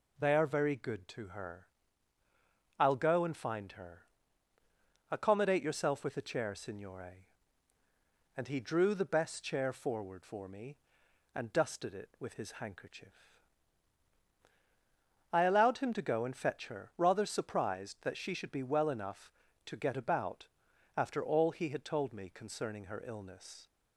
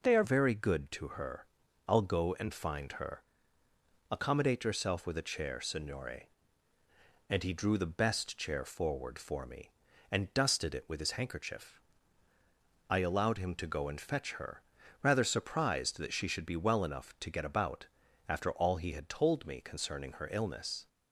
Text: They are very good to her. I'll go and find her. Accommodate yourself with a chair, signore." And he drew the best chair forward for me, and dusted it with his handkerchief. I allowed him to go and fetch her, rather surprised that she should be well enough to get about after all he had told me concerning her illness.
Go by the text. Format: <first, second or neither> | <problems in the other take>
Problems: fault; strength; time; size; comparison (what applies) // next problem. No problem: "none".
first | changes voice at "very"; from 0.2 s on; 20.6 s long // pauses between "about" and "after"; at 17.8 s; 0.42 s long; noticeable in the first